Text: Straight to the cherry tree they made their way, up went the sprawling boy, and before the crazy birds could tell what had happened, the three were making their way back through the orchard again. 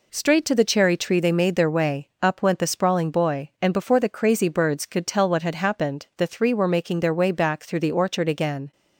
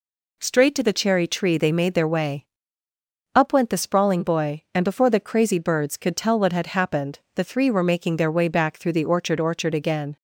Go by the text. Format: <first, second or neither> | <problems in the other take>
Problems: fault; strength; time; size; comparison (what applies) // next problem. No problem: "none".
first | says "orchard" twice; at 9.3 s